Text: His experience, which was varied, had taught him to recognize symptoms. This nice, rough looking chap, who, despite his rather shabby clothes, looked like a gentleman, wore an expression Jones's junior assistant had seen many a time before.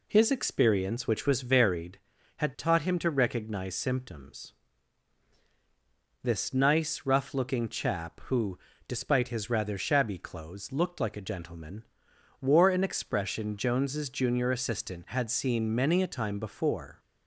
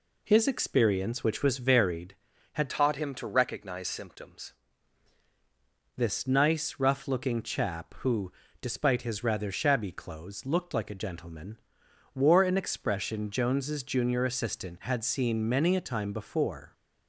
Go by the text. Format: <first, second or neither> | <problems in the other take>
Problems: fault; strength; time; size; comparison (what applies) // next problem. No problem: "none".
first | changes voice from "taught" to "symptoms"; from 2.6 to 4.5 s; 1.9 s long